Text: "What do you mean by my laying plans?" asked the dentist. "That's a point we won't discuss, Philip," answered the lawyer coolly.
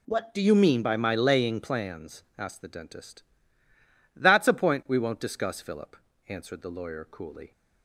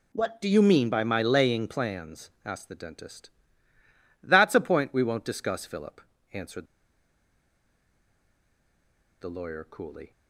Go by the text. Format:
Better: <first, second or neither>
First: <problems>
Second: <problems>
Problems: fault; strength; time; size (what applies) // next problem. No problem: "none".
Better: first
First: none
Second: pauses between "answered" and "the"; strong; at 6.6 s; 2.5 s long